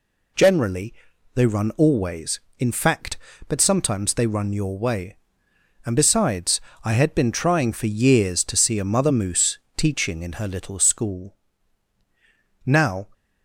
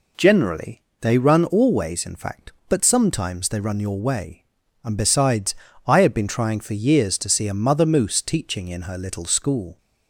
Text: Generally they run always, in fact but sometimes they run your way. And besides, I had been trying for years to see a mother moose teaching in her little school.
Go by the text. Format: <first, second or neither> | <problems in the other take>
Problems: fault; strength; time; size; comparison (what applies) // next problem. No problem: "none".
second | pauses between "Generally" and "they"; at 0.9 s; 0.40 s long; slight in the second // pauses between "moose" and "teaching"; slight; at 9.5 s; 0.18 s long // goes on to say "Now"; slight; from 12.6 s on; 0.42 s long